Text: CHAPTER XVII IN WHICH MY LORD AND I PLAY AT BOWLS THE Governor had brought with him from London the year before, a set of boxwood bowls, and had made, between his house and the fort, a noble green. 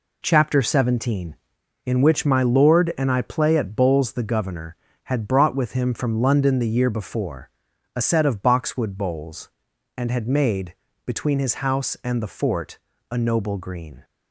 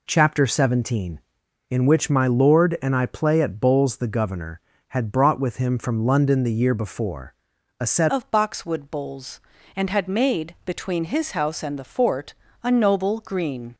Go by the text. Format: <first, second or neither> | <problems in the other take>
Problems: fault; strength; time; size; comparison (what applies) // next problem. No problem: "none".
first | changes voice at "of"; from 8.1 s on; 5.6 s long